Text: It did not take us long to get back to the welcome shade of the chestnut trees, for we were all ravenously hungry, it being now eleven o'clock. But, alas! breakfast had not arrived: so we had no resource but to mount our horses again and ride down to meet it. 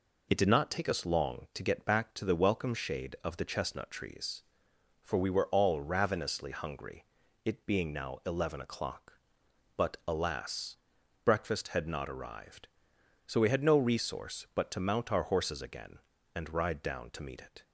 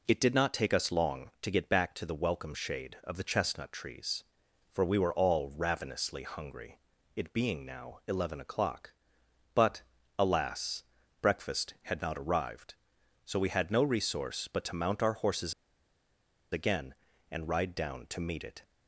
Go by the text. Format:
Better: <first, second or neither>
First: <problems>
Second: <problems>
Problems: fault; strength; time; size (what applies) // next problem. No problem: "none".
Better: first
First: none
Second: pauses between "horses" and "again"; at 15.5 s; 0.99 s long